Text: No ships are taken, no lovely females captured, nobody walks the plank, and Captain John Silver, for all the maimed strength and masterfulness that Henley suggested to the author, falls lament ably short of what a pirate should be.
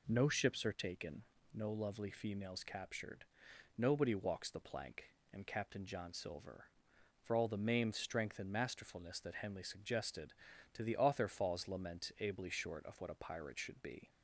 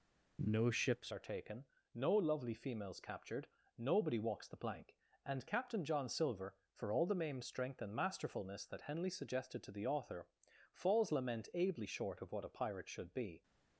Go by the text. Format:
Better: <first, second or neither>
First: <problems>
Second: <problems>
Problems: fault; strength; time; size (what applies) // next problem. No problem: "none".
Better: first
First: none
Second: changes voice at "are"; from 1.1 s on; 12.3 s long